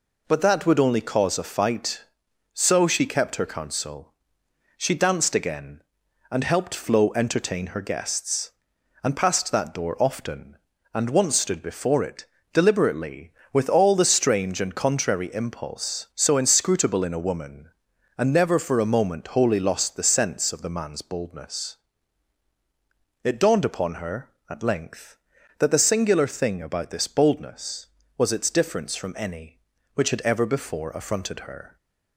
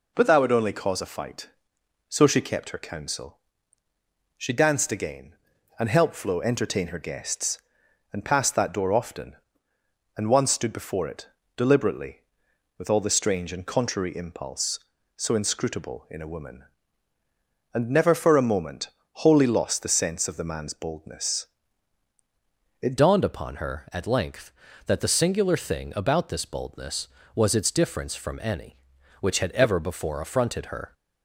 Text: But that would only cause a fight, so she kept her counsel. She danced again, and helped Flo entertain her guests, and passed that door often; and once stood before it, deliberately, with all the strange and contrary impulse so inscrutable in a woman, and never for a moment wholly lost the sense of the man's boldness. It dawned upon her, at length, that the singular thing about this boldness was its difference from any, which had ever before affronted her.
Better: first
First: none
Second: pauses between "moment" and "wholly"; slight; at 18.8 s; 0.26 s long // changes voice at "dawned"; from 22.9 s on; 8.0 s long

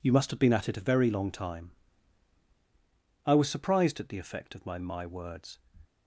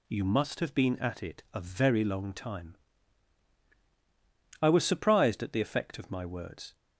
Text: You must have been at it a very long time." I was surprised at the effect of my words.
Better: second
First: says "my" twice; at 4.7 s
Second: none

